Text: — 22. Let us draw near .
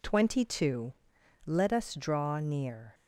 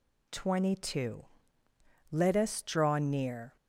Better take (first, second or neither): neither